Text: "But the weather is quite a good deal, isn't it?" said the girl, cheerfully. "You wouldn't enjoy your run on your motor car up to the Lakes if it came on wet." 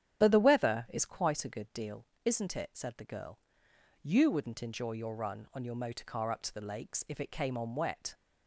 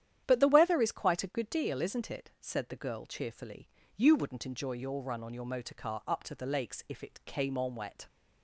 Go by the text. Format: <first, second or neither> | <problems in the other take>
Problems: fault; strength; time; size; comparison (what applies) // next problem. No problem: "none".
second | starts louder than the rest; strong; until 1.2 s; 9.5 dB; strong in the second // skips "cheerfully"; at 3.7 s